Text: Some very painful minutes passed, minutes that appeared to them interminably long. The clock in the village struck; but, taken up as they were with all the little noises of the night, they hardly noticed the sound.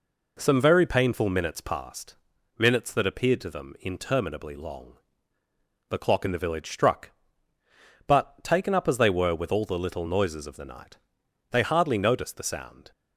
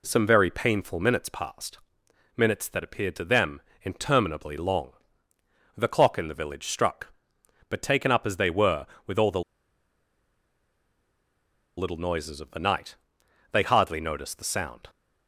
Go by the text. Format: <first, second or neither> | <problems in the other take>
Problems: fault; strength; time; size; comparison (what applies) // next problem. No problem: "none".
first | pauses between "them" and "interminably"; slight; at 3.6 s; 0.18 s long // pauses between "the" and "little"; strong; at 9.4 s; 2.3 s long